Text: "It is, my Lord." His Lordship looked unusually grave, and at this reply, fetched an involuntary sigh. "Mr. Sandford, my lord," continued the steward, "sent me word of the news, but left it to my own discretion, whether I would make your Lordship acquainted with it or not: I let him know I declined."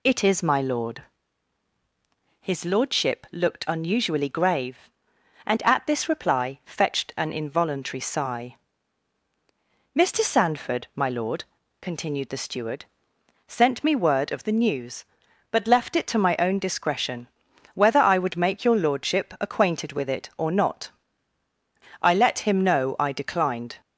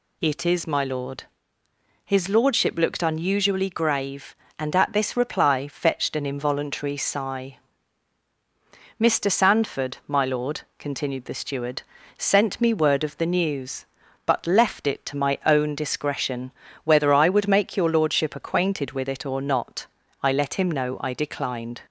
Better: neither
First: none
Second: none

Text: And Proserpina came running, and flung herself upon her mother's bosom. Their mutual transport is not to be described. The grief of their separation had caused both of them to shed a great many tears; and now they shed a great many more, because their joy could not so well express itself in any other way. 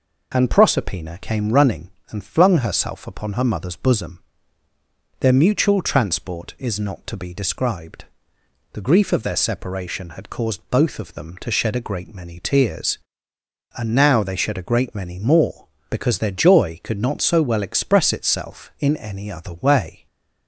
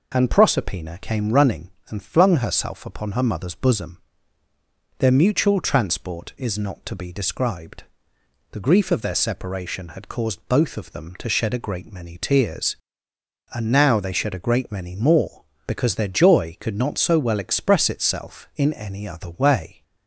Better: neither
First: none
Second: none

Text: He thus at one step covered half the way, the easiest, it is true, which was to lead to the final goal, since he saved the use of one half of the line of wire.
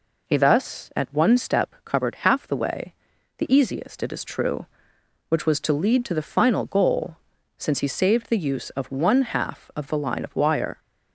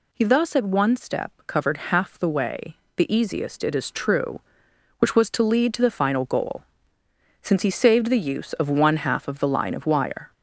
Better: first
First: none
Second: gets louder; slight; throughout; 2.5 dB

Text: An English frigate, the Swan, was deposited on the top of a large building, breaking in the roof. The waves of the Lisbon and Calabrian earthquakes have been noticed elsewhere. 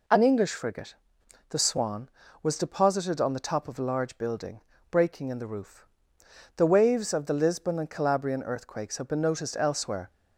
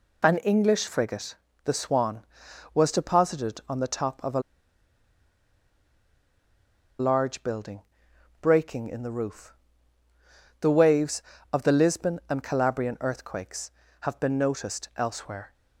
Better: first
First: none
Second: pauses between "a" and "large"; strong; at 4.3 s; 2.5 s long

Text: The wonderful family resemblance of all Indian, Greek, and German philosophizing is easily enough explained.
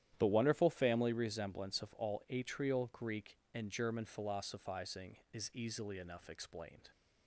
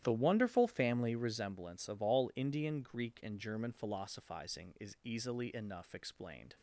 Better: second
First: starts louder than the rest; strong; until 1.1 s; 11 dB // says "Atrial" for "Indian"; at 2.3 s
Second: starts louder than the rest; strong; until 1.0 s; 12.5 dB

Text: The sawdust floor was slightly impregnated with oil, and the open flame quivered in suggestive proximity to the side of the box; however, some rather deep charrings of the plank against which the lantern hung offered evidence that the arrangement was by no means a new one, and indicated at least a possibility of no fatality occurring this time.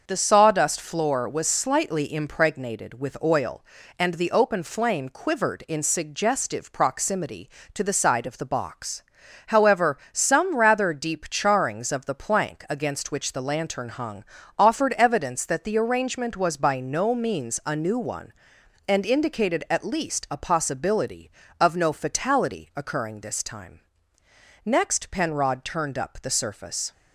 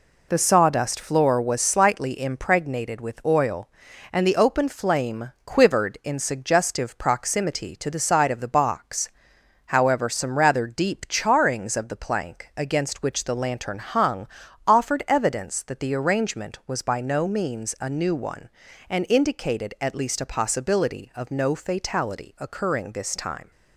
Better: second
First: starts louder than the rest; until 1.0 s; 6.5 dB // pauses between "hung" and "offered"; slight; at 14.2 s; 0.36 s long // goes on to say "Next Penrod turned up the surface"; strong; from 24.6 s on; 2.2 s long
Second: pauses between "hung" and "offered"; at 14.2 s; 0.40 s long

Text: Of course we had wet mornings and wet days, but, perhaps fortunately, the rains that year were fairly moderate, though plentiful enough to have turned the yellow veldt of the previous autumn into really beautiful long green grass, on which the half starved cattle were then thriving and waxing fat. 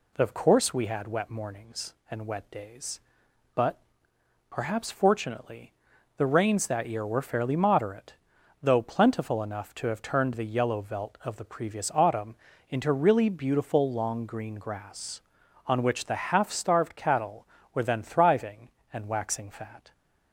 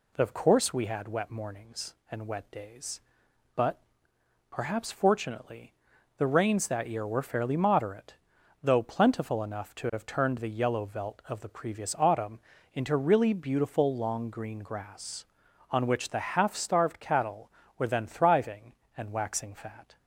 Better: neither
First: pauses between "autumn" and "into"; slight; at 12.3 s; 0.34 s long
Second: pauses between "autumn" and "into"; slight; at 12.3 s; 0.34 s long

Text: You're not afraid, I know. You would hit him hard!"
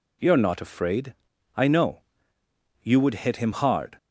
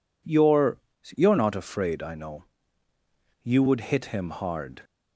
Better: first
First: none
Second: says "You're" twice; at 1.1 s

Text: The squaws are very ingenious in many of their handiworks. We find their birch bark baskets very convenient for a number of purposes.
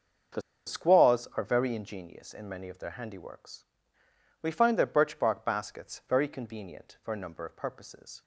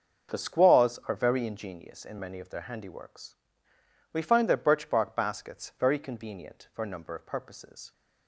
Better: second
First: starts louder than the rest; until 1.6 s; 6.5 dB // pauses between "The" and "squaws"; slight; at 0.4 s; 0.25 s long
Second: starts louder than the rest; until 1.3 s; 6.5 dB

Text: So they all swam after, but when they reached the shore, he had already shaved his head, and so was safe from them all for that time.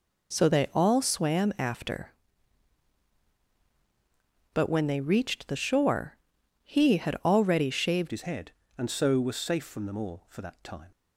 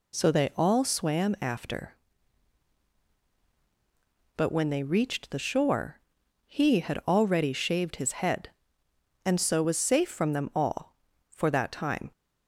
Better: second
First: changes voice at "his"; from 8.1 s on; 2.8 s long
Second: none

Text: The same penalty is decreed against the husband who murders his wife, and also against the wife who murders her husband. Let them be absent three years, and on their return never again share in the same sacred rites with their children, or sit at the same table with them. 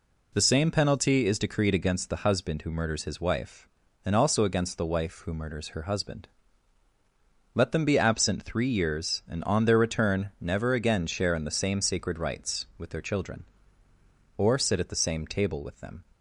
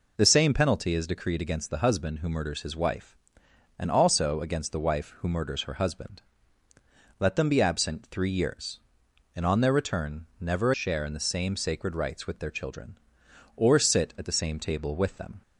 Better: first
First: none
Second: skips "again"; at 10.7 s

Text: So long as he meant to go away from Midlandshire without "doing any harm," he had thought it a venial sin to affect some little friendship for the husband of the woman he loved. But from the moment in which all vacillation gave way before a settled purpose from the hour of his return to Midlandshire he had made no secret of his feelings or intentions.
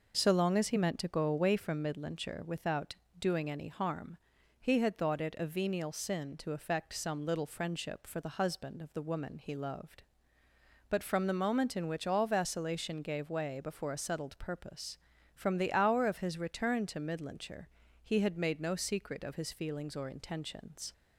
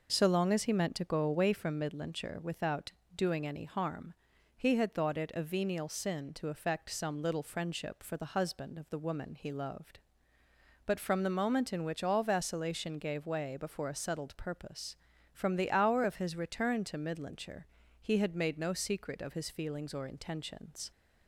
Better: neither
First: pauses between "without" and "doing"; slight; at 2.9 s; 0.24 s long // pauses between "Midlandshire" and "he"; slight; at 17.6 s; 0.34 s long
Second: pauses between "without" and "doing"; slight; at 2.9 s; 0.24 s long // pauses between "Midlandshire" and "he"; slight; at 17.6 s; 0.34 s long

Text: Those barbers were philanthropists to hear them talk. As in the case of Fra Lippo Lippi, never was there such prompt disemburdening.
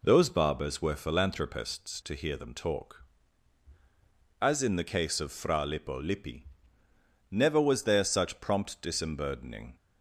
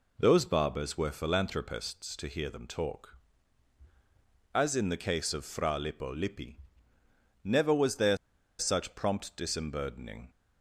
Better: first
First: none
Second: pauses between "there" and "such"; at 8.1 s; 0.42 s long

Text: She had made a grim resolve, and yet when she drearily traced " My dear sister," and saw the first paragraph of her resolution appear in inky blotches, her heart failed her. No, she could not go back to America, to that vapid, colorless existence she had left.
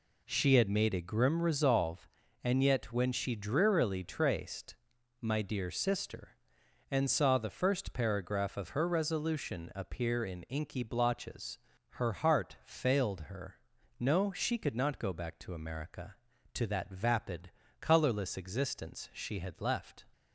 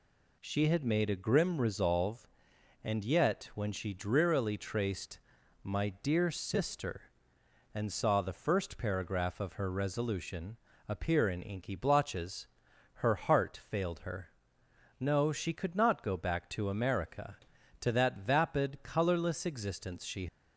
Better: first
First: none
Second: pauses between "resolution" and "appear"; slight; at 10.5 s; 0.30 s long // stops before "had left"; at 20.2 s

